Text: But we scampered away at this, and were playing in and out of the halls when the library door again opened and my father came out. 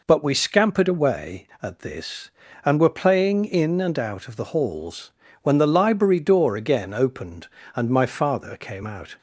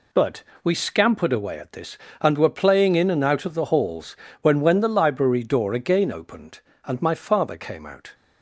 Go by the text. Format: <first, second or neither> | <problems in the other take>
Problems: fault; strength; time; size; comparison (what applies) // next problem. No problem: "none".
first | pauses between "But" and "we"; slight; at 0.4 s; 0.18 s long // pauses between "halls" and "when"; slight; at 4.1 s; 0.26 s long; slight in the first // says "when" twice; at 4.5 s